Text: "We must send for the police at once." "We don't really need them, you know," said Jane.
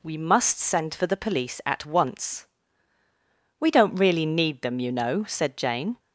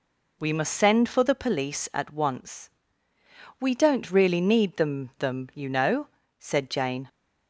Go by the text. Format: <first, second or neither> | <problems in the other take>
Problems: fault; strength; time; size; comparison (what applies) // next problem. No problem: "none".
first | says "them" twice; at 5.1 s